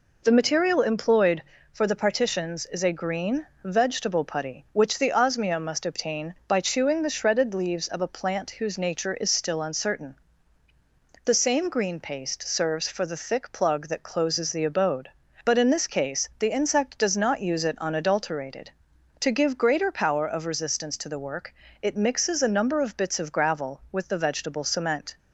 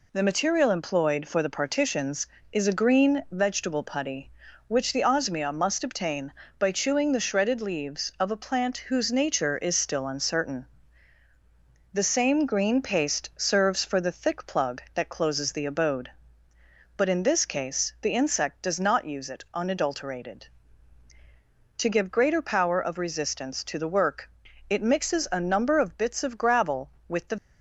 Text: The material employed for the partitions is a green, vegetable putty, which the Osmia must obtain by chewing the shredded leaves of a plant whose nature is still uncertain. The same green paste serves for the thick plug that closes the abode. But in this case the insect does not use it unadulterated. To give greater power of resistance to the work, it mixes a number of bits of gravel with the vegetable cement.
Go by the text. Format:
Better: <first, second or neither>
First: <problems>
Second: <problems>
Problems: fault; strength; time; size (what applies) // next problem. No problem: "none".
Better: first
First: none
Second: stops before "vegetable cement"; at 27.3 s